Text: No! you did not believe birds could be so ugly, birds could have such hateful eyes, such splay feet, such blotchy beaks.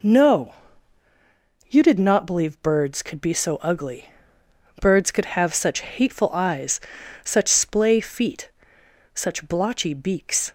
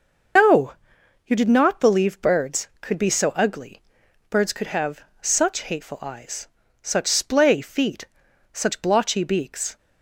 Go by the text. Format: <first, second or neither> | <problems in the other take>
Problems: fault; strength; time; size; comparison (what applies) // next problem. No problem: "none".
first | loses the start of "No"; at 0.3 s; 90 ms // starts louder than the rest; until 1.9 s; 6 dB // pauses between "have" and "such"; slight; at 5.0 s; 0.18 s long